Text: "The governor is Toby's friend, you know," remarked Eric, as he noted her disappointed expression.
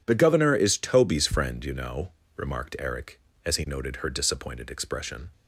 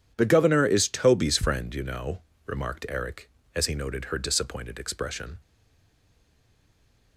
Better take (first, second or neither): first